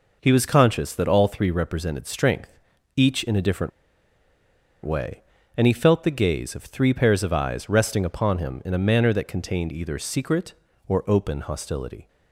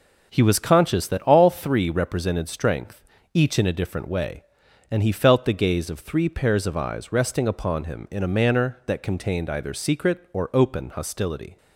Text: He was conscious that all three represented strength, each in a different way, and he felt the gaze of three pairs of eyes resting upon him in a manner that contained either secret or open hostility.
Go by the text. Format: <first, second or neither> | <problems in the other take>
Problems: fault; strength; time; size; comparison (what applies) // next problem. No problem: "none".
second | pauses between "different" and "way"; at 3.7 s; 1.1 s long